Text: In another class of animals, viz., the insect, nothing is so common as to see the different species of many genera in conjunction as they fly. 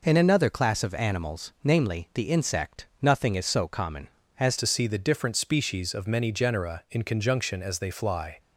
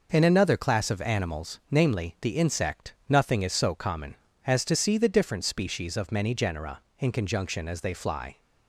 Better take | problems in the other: second | changes voice at "to"; from 4.5 s on; 3.8 s long

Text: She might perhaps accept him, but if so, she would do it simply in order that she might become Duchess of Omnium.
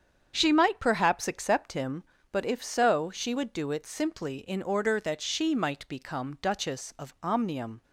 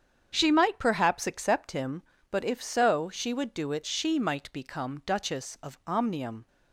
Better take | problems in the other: first | starts louder than the rest; strong; until 1.3 s; 8 dB; strong in the first // skips "simply in order that"; at 3.8 s

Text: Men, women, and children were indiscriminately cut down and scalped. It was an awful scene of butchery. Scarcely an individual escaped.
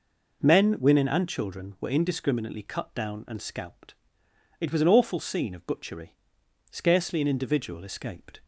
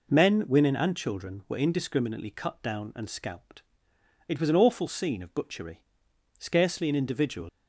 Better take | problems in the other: first | stops before "escaped"; at 7.4 s

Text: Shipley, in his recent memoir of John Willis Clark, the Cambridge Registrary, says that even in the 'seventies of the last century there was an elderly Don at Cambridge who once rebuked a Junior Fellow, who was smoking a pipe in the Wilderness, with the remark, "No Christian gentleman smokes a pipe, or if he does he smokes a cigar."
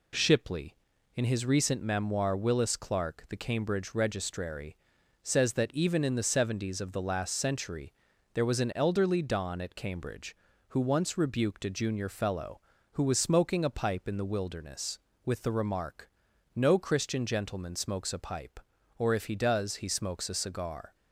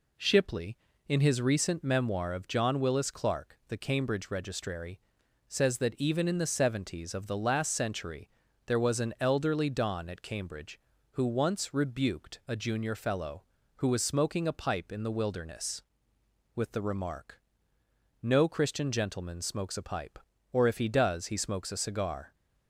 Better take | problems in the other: second | skips "of John"; at 2.3 s // pauses between "century" and "there"; at 7.9 s; 0.42 s long; slight in the second

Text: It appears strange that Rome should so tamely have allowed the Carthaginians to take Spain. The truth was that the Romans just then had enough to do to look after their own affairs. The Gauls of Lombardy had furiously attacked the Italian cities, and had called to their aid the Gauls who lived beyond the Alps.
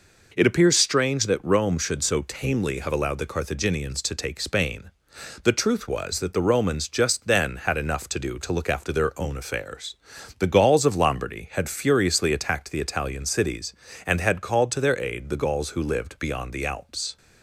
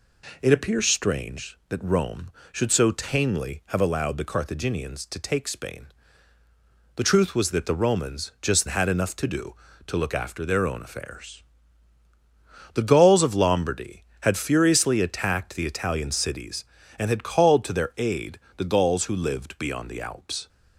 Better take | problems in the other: first | skips "then"; at 8.6 s // pauses between "aid" and "the"; slight; at 18.3 s; 0.16 s long

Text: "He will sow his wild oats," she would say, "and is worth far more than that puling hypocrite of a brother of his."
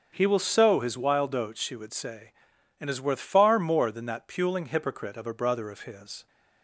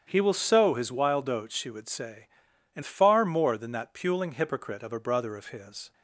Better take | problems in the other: first | starts louder than the rest; strong; until 1.0 s; 8.5 dB; also in the first // skips "is worth"; at 2.8 s

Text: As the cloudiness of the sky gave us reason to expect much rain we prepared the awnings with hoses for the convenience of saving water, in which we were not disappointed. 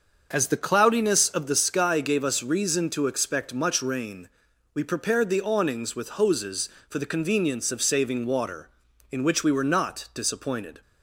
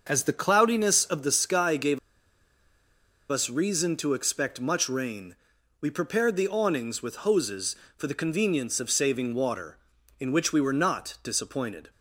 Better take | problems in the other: first | starts louder than the rest; until 1.0 s; 6.5 dB; also in the first // pauses between "gave" and "us"; strong; at 1.9 s; 1.3 s long // pauses between "rain" and "we"; at 5.3 s; 0.44 s long; also in the first

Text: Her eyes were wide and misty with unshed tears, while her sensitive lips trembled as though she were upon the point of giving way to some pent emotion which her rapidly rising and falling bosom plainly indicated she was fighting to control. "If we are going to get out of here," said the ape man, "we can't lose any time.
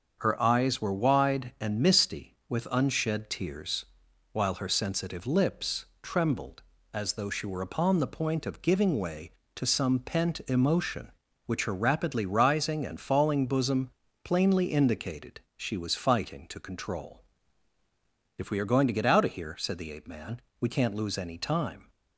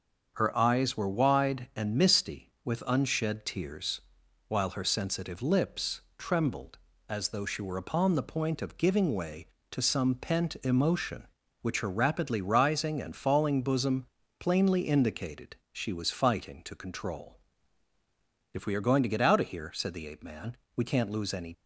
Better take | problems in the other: first | starts louder than the rest; until 1.3 s; 6.5 dB; also in the first // pauses between "lips" and "trembled"; slight; at 6.0 s; 0.18 s long; slight in the first // pauses between "bosom" and "plainly"; slight; at 14.0 s; 0.34 s long; slight in the first // pauses between "indicated" and "she"; slight; at 15.5 s; 0.16 s long; slight in the first // stops before "time"; at 21.5 s

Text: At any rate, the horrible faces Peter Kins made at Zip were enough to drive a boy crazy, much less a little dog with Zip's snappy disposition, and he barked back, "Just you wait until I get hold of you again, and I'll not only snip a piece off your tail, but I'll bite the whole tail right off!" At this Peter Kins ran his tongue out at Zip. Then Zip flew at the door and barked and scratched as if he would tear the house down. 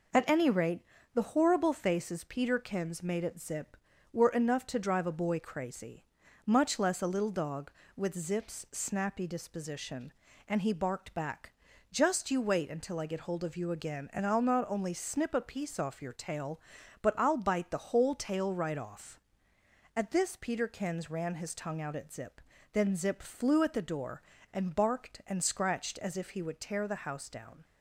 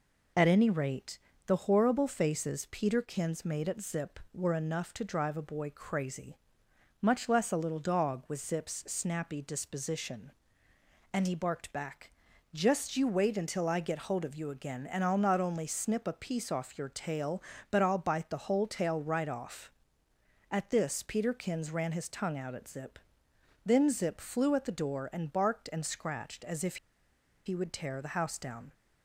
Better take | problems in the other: first | pauses between "if" and "he"; noticeable; at 26.7 s; 0.70 s long

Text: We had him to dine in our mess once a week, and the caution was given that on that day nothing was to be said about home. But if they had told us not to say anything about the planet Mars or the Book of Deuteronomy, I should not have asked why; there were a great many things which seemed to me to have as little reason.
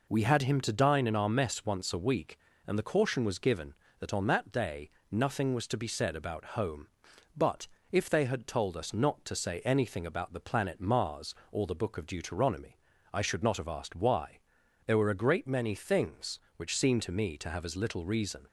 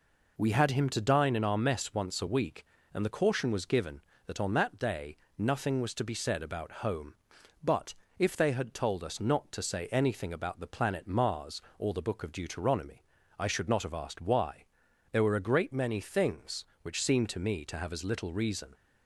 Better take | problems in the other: neither | pauses between "day" and "nothing"; slight; the same in both // pauses between "But" and "if"; slight; the same in both

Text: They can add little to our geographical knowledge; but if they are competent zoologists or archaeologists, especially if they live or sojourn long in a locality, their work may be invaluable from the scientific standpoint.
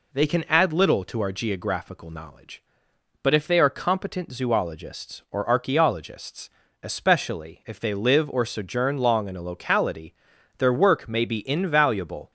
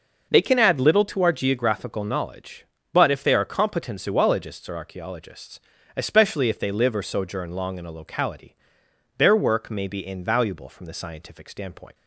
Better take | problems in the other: second | stops before "from the scientific standpoint"; at 12.2 s

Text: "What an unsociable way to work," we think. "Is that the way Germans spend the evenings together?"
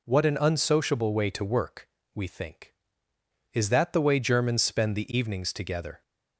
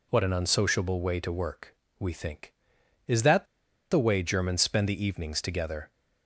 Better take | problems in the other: first | pauses between "that" and "the"; at 3.4 s; 0.45 s long

